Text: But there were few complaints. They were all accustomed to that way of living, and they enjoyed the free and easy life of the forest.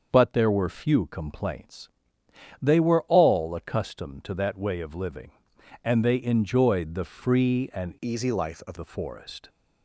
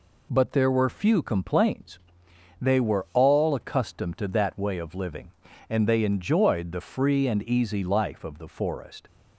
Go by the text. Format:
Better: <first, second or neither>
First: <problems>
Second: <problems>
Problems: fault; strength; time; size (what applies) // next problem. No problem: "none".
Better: second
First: starts louder than the rest; until 1.1 s; 6.5 dB // changes voice from "easy" to "of"; from 8.0 to 8.7 s; 0.7 s long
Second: none